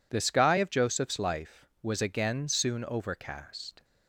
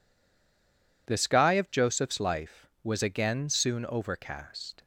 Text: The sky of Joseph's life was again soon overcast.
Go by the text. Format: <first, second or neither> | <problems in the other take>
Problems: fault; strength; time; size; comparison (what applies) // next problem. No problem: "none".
first | stays silent before the first word; until 1.0 s; 1.0 s long